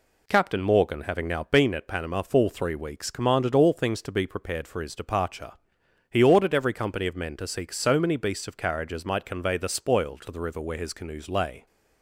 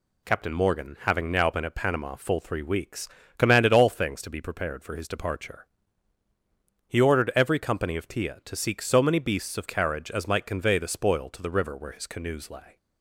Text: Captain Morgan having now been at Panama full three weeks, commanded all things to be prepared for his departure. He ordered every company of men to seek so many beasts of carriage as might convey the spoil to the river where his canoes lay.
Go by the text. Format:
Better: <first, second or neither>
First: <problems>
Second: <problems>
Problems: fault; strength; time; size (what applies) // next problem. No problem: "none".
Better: first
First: none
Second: says "tia" for "men"; at 8.0 s